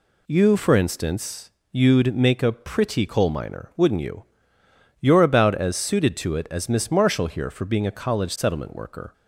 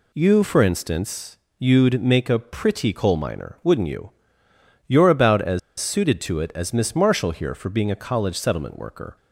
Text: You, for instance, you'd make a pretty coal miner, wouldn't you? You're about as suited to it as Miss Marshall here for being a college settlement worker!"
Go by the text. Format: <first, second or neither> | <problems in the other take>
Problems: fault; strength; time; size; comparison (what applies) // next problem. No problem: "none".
first | pauses between "as" and "suited"; slight; at 5.5 s; 0.19 s long